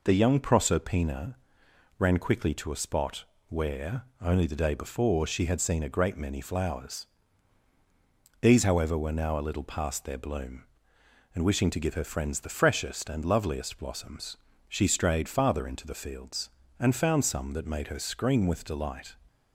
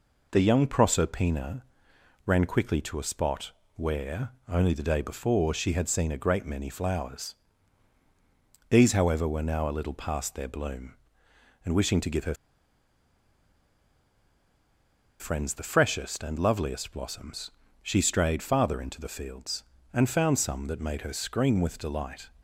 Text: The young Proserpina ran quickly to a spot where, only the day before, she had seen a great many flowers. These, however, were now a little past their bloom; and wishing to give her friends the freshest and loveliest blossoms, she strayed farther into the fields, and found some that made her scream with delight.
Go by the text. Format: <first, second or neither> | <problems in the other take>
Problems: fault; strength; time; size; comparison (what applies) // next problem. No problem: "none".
first | pauses between "Proserpina" and "ran"; noticeable; at 1.6 s; 0.64 s long; noticeable in the first // pauses between "spot" and "where"; slight; at 3.5 s; 0.24 s long; slight in the first // pauses between "her" and "friends"; strong; at 12.3 s; 2.8 s long